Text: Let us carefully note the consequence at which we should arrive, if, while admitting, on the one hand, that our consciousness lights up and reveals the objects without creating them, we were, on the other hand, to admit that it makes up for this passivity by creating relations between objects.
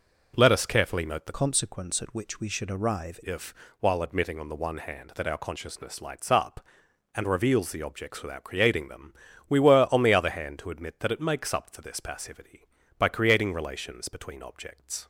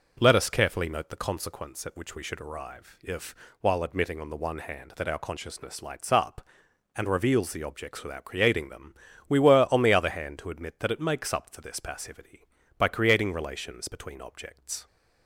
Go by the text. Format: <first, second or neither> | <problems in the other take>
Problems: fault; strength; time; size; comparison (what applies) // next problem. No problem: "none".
second | changes voice from "consequence" to "arrive"; from 1.3 to 3.1 s; 1.8 s long